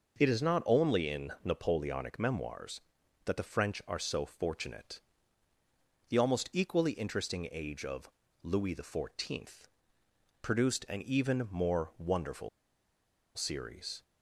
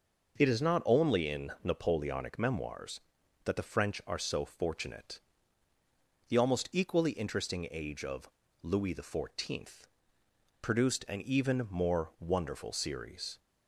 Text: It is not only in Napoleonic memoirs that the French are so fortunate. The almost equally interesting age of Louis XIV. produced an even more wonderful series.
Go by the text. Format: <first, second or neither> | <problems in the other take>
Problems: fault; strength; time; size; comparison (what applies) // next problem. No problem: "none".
second | pauses between "of" and "Louis"; slight; at 8.0 s; 0.34 s long; slight in the second // pauses between "wonderful" and "series"; noticeable; at 12.4 s; 0.86 s long